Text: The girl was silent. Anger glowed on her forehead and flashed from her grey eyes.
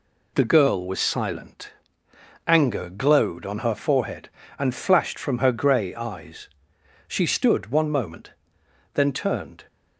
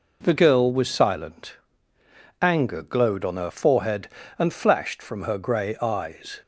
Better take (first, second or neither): second